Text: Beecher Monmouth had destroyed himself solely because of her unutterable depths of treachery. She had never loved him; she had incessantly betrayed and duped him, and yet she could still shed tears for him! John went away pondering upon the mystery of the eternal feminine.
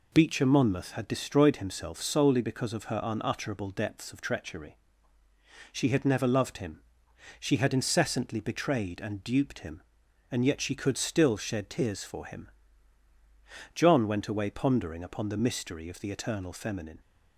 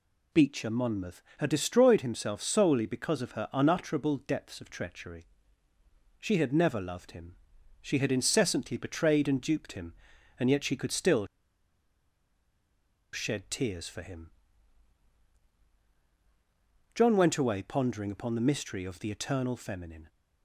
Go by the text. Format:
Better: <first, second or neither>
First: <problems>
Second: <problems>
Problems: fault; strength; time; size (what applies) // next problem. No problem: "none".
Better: first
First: none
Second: pauses between "still" and "shed"; strong; at 11.2 s; 1.8 s long